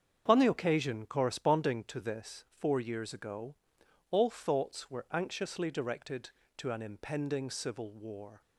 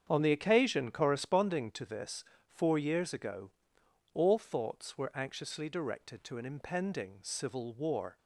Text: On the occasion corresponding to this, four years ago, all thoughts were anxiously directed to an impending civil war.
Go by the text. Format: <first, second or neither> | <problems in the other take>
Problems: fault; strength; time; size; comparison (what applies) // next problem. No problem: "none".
neither | starts louder than the rest; strong; the same in both